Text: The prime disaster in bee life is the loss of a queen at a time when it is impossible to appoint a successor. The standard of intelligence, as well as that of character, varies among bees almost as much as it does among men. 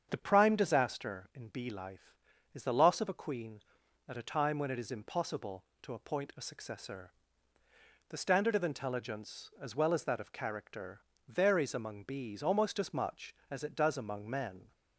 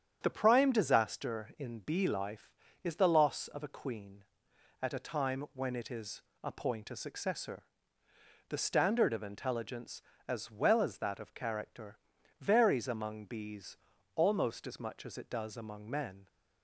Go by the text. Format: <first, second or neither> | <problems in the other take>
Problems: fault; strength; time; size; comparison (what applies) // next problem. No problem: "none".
first | starts louder than the rest; strong; until 1.2 s; 8.5 dB; strong in the first // skips "impossible to"; at 6.3 s // pauses between "bees" and "almost"; at 13.7 s; 0.38 s long